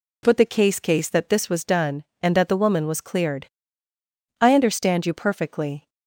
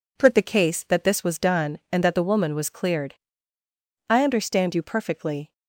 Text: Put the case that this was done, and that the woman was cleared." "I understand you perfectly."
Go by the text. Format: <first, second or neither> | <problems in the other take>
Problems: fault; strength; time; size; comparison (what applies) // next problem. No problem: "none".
second | says "case" twice; at 0.8 s